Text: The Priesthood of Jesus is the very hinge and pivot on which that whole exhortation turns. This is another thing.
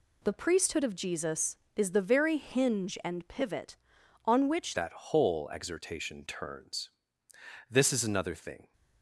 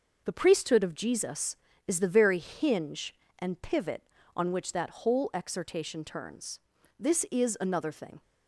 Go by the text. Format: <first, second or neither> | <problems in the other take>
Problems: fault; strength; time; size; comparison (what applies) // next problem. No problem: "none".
second | changes voice at "that"; from 4.7 s on; 4.0 s long